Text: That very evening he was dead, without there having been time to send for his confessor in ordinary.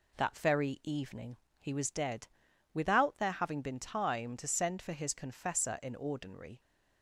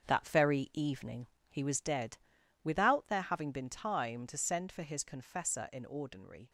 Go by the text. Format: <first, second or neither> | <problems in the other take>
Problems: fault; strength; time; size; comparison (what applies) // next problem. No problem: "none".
first | gets quieter; strong; throughout; 8.5 dB // pauses between "evening" and "he"; slight; at 1.2 s; 0.22 s long; slight in the first